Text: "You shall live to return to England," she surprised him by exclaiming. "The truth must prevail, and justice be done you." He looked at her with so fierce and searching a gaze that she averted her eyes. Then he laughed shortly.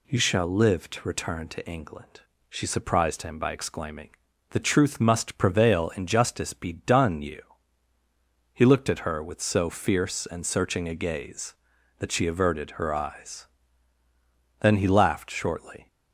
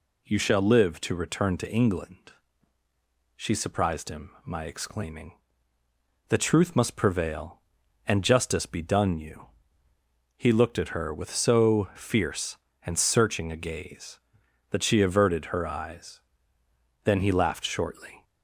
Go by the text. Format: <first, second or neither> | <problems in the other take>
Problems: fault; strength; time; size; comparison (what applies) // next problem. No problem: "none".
first | says "my" for "by"; at 4.4 s